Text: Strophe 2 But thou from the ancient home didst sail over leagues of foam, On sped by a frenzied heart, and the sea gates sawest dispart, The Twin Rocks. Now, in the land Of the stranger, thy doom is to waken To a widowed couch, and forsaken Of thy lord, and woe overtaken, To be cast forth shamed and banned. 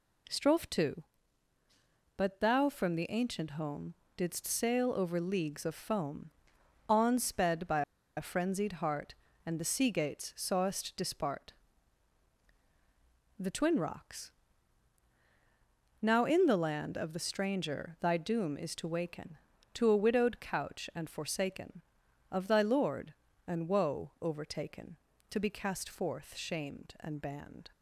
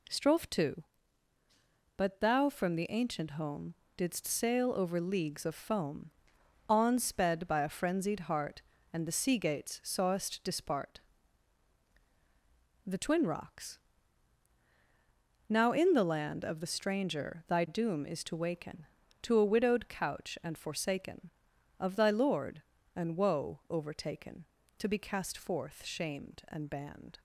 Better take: second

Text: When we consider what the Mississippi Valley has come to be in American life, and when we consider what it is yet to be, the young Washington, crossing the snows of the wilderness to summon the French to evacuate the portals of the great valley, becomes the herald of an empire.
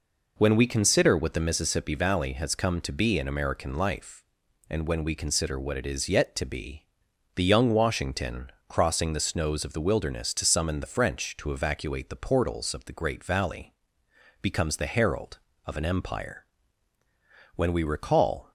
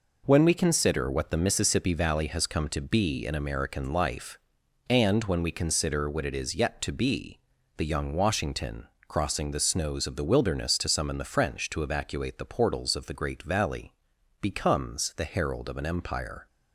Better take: second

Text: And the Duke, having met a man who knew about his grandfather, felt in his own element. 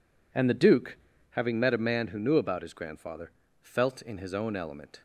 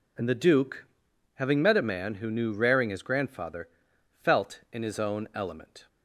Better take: first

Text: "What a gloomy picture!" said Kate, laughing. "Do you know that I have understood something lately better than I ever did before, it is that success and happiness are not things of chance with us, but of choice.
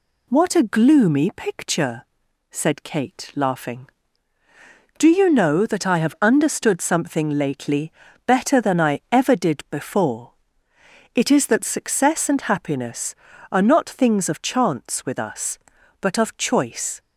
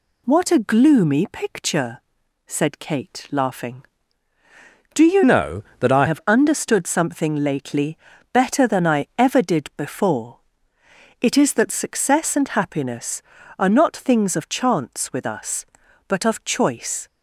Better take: first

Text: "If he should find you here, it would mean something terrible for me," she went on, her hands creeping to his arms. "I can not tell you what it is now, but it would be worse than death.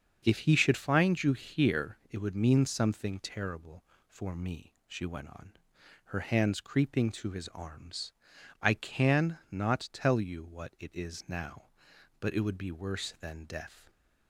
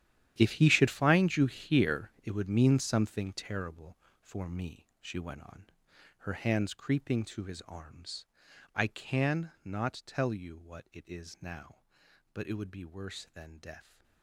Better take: first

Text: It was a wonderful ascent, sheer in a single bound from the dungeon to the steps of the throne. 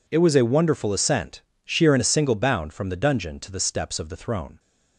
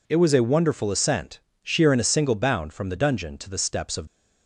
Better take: first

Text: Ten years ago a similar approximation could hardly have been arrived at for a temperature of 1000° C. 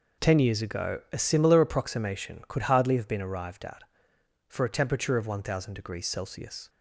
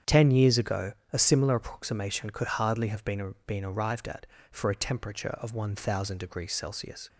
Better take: first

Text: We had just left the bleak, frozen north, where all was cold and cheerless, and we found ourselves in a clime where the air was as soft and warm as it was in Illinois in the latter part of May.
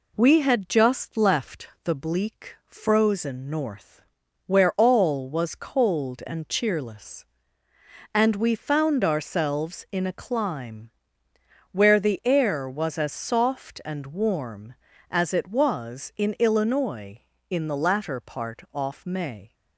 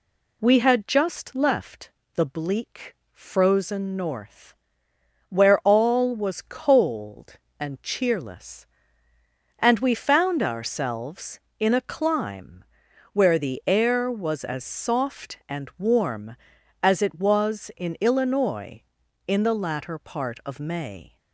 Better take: second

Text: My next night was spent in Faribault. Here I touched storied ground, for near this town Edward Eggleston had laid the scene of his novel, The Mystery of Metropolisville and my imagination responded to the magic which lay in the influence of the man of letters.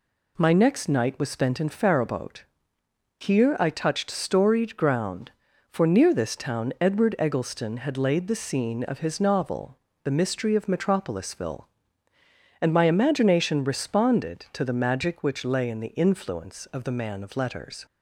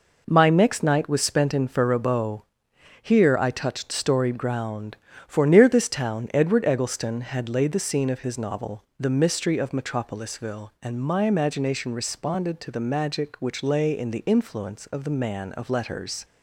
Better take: neither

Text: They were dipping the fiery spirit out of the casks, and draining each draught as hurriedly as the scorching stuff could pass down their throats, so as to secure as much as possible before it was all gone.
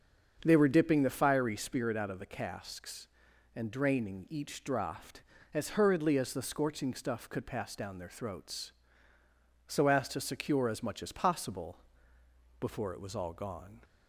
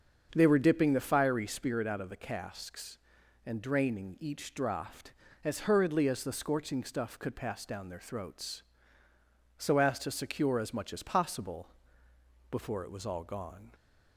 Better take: neither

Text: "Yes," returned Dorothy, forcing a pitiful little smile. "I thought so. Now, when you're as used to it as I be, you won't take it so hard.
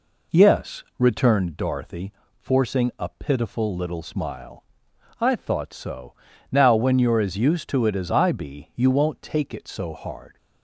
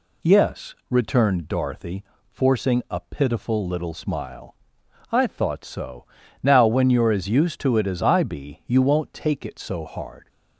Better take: second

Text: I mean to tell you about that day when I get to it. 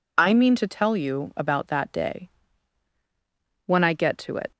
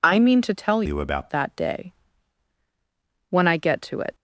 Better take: first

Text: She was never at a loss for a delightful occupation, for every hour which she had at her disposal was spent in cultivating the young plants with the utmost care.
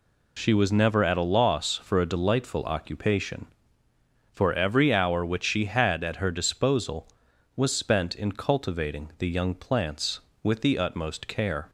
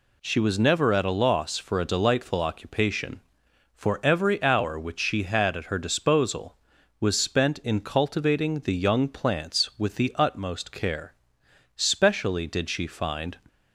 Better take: first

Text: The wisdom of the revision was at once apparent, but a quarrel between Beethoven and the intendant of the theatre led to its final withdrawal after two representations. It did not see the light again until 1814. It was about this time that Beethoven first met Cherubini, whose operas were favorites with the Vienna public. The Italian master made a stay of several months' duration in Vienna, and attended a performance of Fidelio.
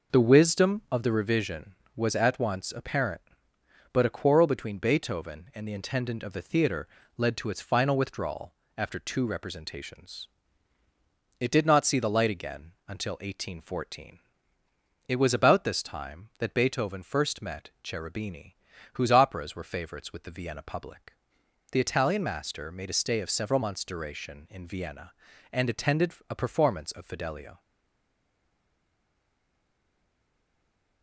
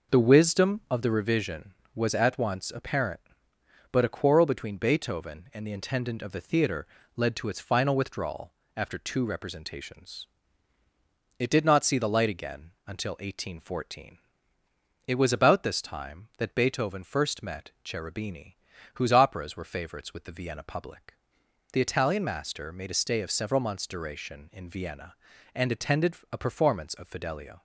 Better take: second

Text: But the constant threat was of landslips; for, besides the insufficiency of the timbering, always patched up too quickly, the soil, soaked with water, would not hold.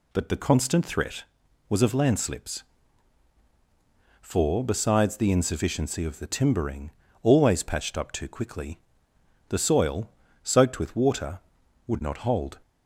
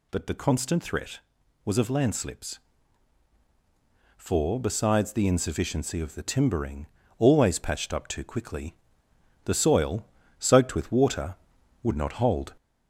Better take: first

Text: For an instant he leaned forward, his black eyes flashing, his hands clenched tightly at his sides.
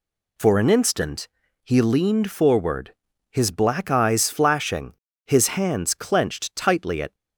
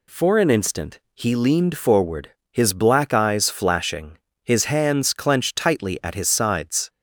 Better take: second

